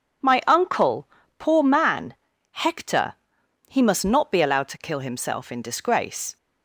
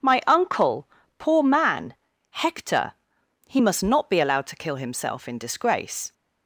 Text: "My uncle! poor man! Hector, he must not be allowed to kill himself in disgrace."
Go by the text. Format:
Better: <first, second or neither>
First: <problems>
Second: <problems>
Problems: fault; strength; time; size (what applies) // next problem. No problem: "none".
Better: neither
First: none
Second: none